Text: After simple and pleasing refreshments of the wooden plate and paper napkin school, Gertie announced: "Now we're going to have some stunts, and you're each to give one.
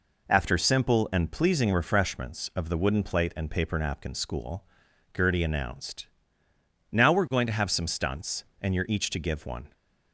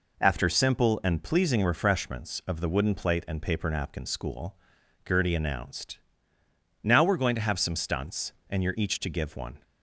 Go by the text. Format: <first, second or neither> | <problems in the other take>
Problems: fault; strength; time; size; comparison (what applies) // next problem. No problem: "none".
neither | none